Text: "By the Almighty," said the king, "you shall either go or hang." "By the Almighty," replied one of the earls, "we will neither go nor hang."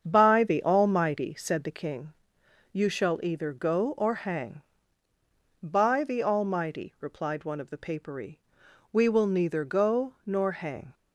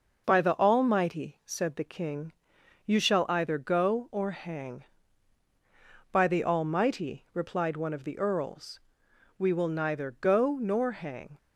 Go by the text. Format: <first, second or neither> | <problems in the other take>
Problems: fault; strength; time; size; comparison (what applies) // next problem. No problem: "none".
second | starts louder than the rest; strong; until 1.0 s; 7.5 dB // says "papery" for "earls"; at 7.7 s